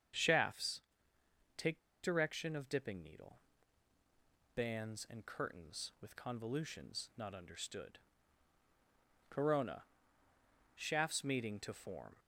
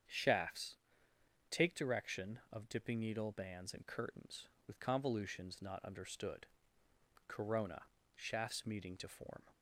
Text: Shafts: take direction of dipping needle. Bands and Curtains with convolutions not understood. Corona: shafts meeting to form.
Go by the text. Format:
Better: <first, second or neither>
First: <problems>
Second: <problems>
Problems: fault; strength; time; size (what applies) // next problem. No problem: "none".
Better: second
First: starts louder than the rest; strong; until 2.1 s; 7.5 dB // pauses between "take" and "direction"; slight; at 1.7 s; 0.26 s long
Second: starts louder than the rest; strong; until 1.8 s; 8 dB